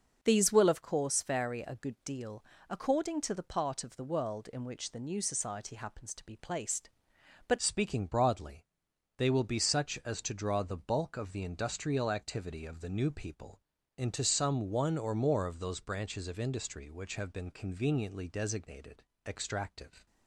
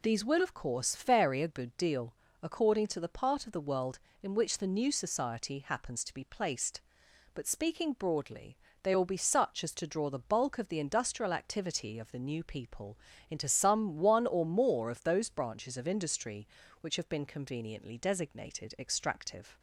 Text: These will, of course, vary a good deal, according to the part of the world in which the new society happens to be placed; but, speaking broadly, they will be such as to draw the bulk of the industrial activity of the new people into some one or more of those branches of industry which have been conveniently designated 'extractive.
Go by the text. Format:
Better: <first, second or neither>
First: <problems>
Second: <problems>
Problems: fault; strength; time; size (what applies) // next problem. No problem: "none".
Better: second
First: starts louder than the rest; until 1.2 s; 6 dB // changes voice at "speaking"; from 7.5 s on; 12.5 s long // pauses between "people" and "into"; at 13.5 s; 0.38 s long // pauses between "designated" and "extractive"; slight; at 19.0 s; 0.22 s long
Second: pauses between "people" and "into"; slight; at 12.9 s; 0.32 s long